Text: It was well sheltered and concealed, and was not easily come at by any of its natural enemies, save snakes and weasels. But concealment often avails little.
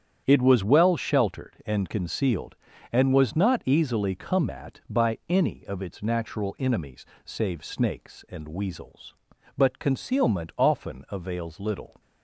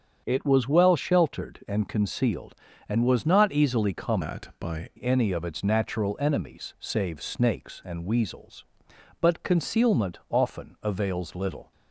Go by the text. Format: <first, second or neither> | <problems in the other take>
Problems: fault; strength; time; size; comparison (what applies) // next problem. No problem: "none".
first | starts louder than the rest; strong; until 1.2 s; 7.5 dB; strong in the first // changes voice from "at" to "by"; from 4.2 to 4.8 s; 0.6 s long